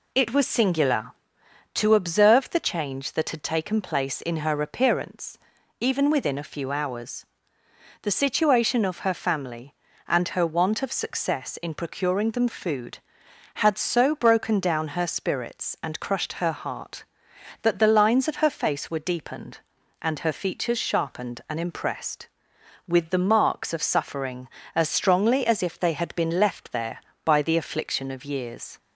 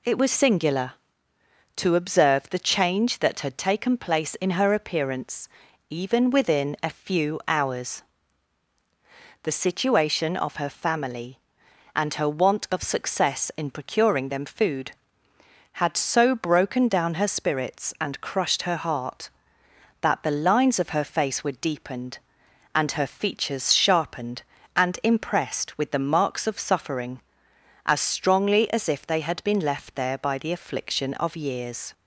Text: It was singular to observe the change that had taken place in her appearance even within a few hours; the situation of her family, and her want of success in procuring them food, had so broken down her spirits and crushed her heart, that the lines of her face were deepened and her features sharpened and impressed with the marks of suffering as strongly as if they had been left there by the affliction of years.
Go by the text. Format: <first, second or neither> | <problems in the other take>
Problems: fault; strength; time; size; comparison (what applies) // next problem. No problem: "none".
neither | pauses between "appearance" and "even"; the same in both